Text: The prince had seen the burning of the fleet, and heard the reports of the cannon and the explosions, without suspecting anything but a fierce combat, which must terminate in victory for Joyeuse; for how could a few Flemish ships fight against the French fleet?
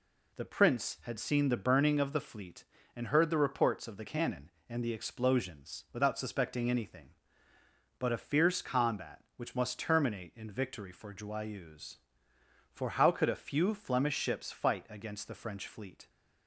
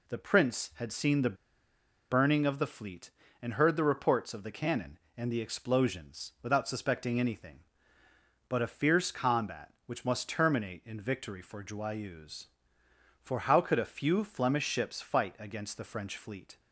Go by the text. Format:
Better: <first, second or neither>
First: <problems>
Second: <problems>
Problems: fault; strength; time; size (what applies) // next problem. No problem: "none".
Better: first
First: none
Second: pauses between "the" and "burning"; noticeable; at 1.3 s; 0.76 s long